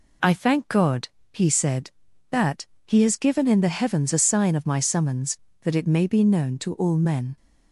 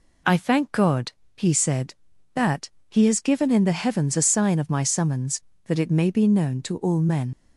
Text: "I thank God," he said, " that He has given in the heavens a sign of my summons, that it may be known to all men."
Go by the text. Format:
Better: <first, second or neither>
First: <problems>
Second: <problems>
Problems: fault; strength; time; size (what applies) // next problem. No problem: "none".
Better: first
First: pauses between "that" and "He"; slight; at 2.6 s; 0.20 s long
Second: pauses between "that" and "He"; slight; at 2.6 s; 0.20 s long // leaves "men" unfinished; at 7.3 s; 65 ms